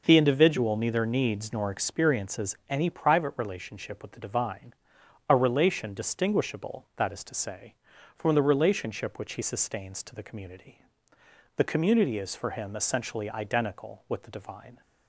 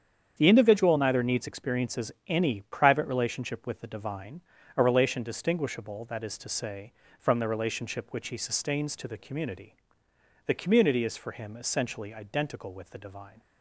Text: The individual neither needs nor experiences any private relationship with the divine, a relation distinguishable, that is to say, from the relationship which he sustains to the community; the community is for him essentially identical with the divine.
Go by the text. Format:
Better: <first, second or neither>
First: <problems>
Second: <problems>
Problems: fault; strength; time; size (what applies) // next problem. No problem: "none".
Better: first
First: none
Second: starts louder than the rest; strong; until 1.4 s; 8 dB // skips "nor"; at 1.4 s // pauses between "experiences" and "any"; slight; at 2.1 s; 0.16 s long